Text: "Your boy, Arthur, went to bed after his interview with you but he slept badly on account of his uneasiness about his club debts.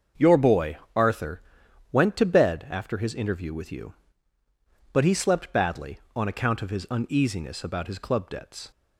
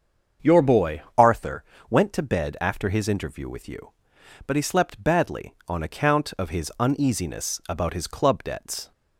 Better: first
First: starts louder than the rest; until 1.3 s; 6.5 dB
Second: starts louder than the rest; until 1.5 s; 7 dB // changes voice at "Arthur"; from 1.1 s on; 7.8 s long

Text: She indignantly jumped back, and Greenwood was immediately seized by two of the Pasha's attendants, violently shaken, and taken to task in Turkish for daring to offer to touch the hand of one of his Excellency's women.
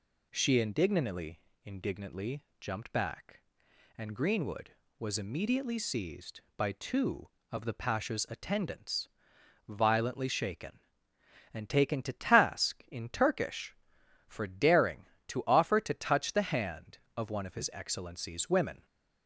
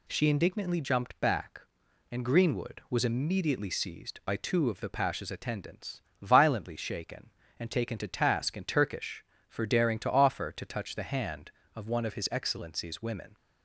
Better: second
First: says "indignantly" twice; at 1.6 s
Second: none

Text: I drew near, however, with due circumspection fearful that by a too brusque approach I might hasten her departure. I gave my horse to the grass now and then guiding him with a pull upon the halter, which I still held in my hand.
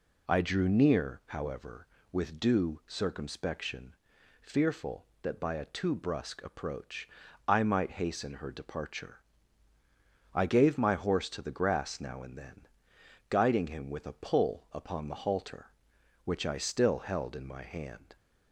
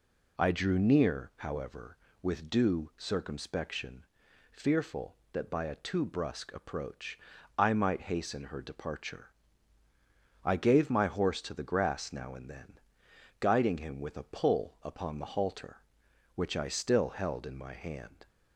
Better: neither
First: pauses between "circumspection" and "fearful"; noticeable; at 3.9 s; 0.48 s long // pauses between "approach" and "I"; at 7.0 s; 0.40 s long // pauses between "then" and "guiding"; noticeable; at 12.6 s; 0.60 s long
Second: pauses between "circumspection" and "fearful"; noticeable; at 4.0 s; 0.48 s long // pauses between "approach" and "I"; at 7.1 s; 0.40 s long // pauses between "then" and "guiding"; noticeable; at 12.7 s; 0.58 s long

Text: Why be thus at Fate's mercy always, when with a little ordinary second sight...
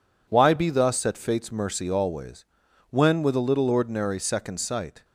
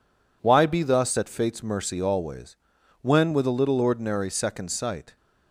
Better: neither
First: none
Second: none

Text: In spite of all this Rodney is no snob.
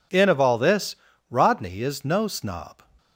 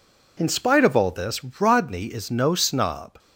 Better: second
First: skips "spite"; at 0.2 s // pauses between "this" and "Rodney"; slight; at 0.9 s; 0.36 s long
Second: pauses between "this" and "Rodney"; slight; at 1.4 s; 0.18 s long

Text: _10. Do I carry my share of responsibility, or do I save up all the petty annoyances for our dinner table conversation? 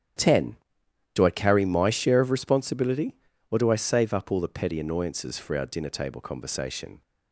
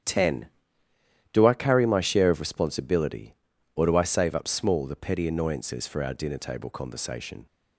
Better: first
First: starts louder than the rest; strong; until 1.7 s; 9.5 dB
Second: starts louder than the rest; strong; until 1.9 s; 9.5 dB // says "small" for "all"; at 4.4 s

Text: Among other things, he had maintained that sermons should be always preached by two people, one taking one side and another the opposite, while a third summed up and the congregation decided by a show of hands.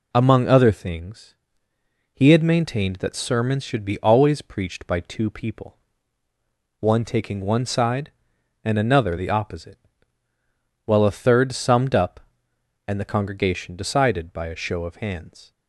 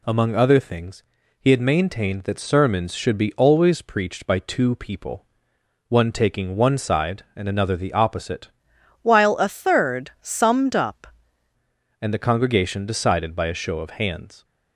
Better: first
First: none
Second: changes voice from "while" to "up"; from 9.0 to 11.0 s; 2.0 s long

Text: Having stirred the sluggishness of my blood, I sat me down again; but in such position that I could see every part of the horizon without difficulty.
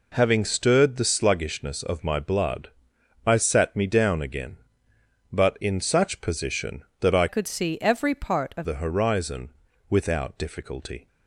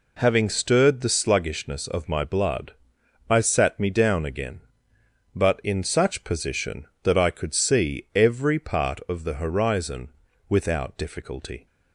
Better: second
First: changes voice from "could" to "of"; from 7.2 to 8.6 s; 1.4 s long // pauses between "horizon" and "without"; at 9.4 s; 0.40 s long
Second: pauses between "horizon" and "without"; at 10.0 s; 0.40 s long

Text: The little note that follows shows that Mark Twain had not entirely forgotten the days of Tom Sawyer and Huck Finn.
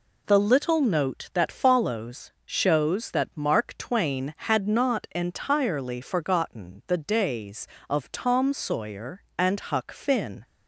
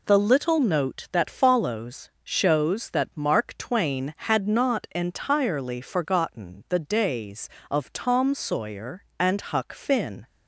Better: neither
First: none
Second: none

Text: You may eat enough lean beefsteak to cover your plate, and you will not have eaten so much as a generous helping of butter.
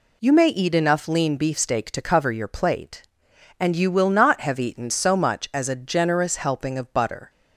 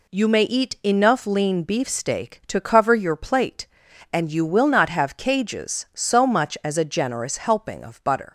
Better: first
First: none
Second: says "cages" for "eaten"; at 5.1 s

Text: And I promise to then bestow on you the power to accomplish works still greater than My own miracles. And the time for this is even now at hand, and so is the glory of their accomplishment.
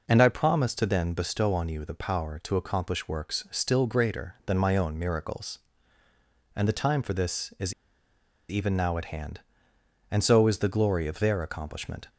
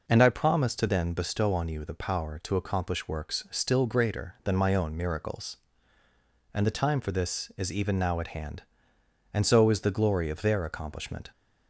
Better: second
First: pauses between "is" and "even"; noticeable; at 7.7 s; 0.76 s long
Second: none

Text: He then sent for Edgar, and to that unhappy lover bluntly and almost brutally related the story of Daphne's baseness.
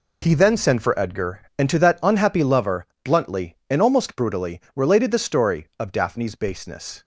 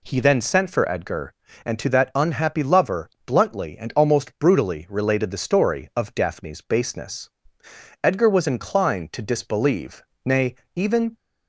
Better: first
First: pauses between "lover" and "bluntly"; slight; at 2.8 s; 0.18 s long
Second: pauses between "lover" and "bluntly"; slight; at 3.0 s; 0.16 s long // goes on to say "Edgar was inclined to disbelieve nay even"; strong; from 8.0 s on; 3.1 s long

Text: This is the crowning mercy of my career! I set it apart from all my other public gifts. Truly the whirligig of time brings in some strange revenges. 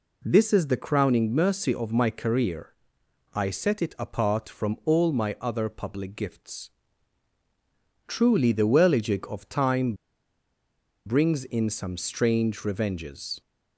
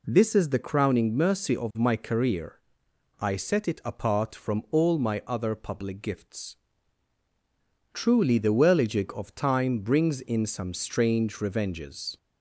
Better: second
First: pauses between "time" and "brings"; at 9.9 s; 1.1 s long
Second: none

